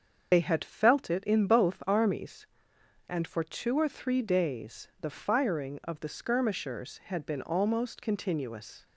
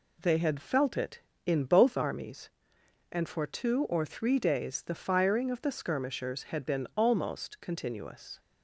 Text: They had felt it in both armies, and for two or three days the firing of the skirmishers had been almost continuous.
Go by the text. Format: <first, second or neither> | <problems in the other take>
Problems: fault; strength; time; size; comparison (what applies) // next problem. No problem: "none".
second | loses the start of "They"; at 0.3 s; 70 ms // starts louder than the rest; until 1.3 s; 6.5 dB